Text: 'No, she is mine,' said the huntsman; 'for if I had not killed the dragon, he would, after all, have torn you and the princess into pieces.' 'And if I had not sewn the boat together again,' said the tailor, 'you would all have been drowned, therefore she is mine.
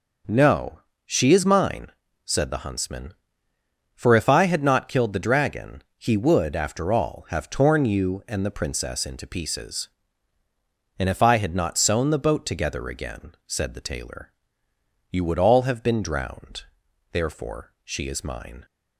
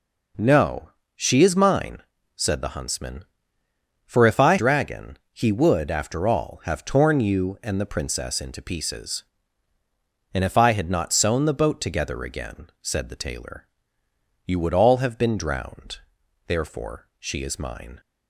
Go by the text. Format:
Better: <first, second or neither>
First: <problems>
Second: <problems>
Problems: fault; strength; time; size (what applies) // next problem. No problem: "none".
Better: first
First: none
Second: skips "had not killed the"; at 4.5 s